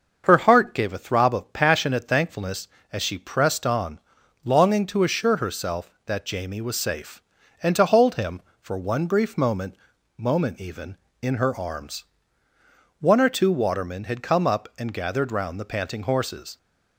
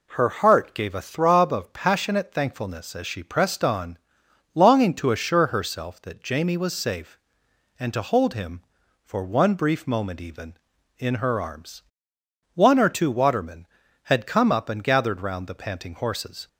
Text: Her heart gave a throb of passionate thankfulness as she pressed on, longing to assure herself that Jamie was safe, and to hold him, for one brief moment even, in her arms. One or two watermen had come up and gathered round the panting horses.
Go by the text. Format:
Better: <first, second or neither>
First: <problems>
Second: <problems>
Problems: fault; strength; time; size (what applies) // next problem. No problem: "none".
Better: second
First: starts louder than the rest; until 1.2 s; 6.5 dB // says "moment" twice; at 10.1 s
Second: none